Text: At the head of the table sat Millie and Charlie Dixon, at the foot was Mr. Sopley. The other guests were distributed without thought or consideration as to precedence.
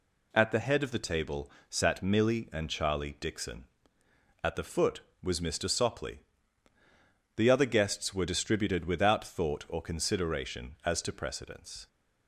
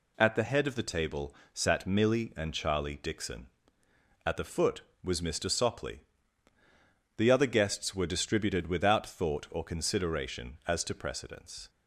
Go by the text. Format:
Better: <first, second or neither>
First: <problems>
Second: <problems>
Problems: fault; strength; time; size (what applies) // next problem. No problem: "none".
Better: neither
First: pauses between "table" and "sat"; slight; at 1.5 s; 0.18 s long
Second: pauses between "table" and "sat"; slight; at 1.3 s; 0.18 s long